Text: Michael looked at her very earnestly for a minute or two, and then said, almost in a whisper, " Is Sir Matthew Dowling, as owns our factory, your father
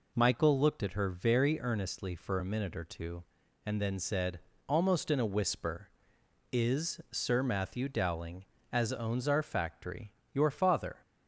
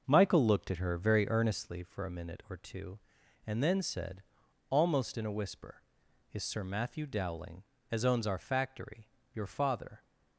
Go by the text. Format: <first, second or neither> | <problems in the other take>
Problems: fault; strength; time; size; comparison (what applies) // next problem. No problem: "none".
first | starts louder than the rest; noticeable; until 1.7 s; 6 dB